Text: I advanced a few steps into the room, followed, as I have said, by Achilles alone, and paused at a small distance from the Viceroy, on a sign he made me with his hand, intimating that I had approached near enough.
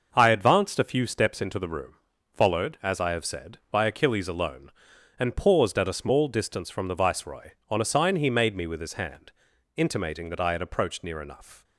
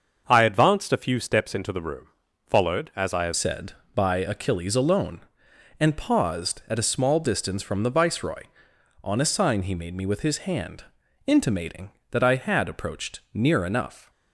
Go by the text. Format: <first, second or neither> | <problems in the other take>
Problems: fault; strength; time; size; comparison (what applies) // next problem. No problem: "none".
first | starts louder than the rest; until 1.2 s; 6.5 dB // changes voice at "said"; from 3.3 s on; 10.7 s long